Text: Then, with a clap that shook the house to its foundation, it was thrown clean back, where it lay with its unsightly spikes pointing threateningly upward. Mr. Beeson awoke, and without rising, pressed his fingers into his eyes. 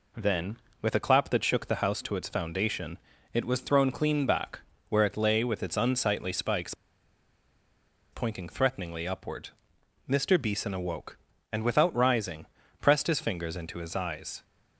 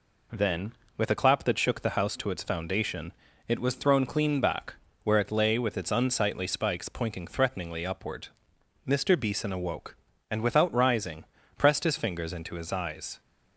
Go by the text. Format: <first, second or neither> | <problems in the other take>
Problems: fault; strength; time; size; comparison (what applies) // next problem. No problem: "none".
second | pauses between "spikes" and "pointing"; strong; at 6.7 s; 1.3 s long